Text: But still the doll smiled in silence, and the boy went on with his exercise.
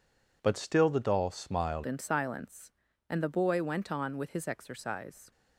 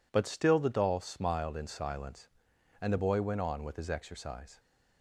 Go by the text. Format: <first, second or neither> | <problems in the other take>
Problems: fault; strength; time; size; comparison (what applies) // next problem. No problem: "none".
second | changes voice at "in"; from 1.8 s on; 3.5 s long